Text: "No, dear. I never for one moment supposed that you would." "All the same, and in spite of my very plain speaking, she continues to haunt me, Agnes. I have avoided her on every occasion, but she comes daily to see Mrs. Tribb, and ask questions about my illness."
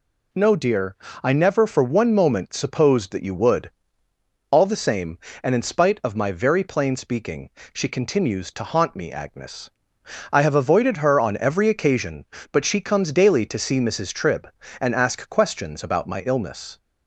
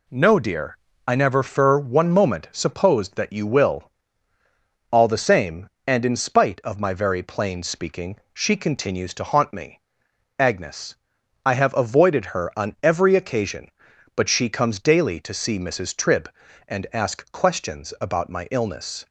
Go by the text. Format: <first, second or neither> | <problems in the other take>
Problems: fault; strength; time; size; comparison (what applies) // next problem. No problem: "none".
first | says "will" for "would"; at 3.4 s